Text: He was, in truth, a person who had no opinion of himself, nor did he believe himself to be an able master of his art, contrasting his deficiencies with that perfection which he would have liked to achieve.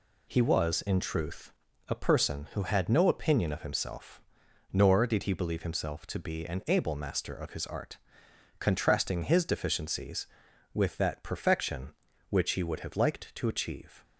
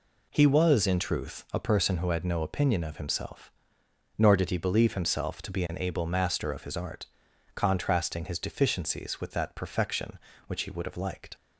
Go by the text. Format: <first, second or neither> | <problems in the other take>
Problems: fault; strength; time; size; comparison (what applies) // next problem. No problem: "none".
first | stops before "to achieve"; at 11.3 s